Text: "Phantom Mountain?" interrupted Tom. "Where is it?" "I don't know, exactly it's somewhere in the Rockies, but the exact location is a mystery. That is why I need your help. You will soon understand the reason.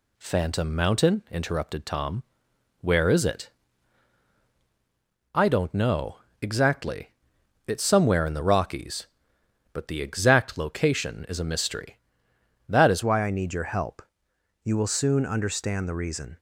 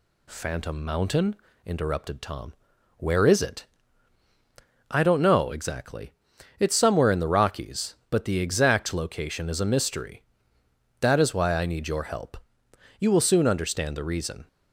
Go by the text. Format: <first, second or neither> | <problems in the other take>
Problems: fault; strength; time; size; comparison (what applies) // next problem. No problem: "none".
second | pauses between "exactly" and "it's"; noticeable; at 7.1 s; 0.56 s long; noticeable in the second // changes voice at "why"; from 13.0 s on; 3.3 s long